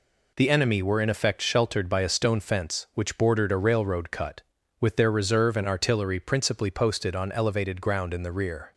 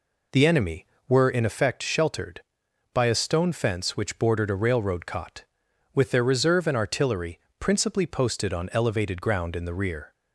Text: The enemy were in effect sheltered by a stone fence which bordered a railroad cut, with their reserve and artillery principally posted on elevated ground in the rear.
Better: first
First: none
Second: says "cot" for "cut"; at 5.0 s // pauses between "artillery" and "principally"; slight; at 7.3 s; 0.20 s long

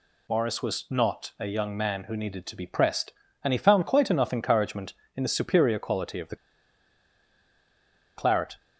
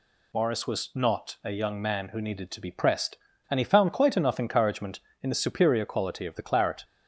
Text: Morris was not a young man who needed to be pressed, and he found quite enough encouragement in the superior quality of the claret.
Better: second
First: pauses between "the" and "claret"; strong; at 6.3 s; 1.8 s long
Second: none

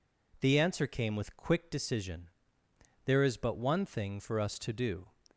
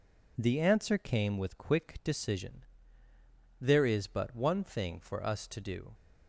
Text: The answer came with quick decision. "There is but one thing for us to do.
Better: neither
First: none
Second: none

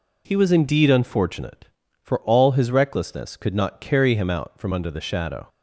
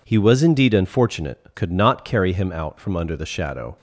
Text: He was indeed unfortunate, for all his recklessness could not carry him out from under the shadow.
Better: first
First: none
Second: skips "for all his recklessness"; at 1.5 s

